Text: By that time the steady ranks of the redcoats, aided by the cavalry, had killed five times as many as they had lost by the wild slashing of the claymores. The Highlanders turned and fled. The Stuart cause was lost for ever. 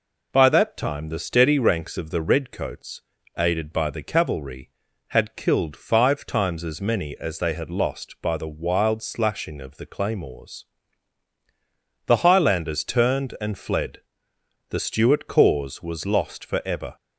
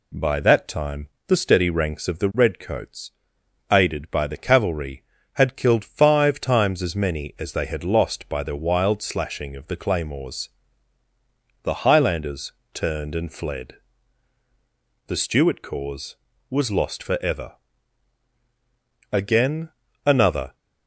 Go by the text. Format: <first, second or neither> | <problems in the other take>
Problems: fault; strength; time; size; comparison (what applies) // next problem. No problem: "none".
first | pauses between "time" and "the"; slight; at 1.0 s; 0.18 s long // pauses between "Highlanders" and "turned"; slight; at 12.5 s; 0.20 s long // goes on to say "Again another"; from 19.1 s on; 1.4 s long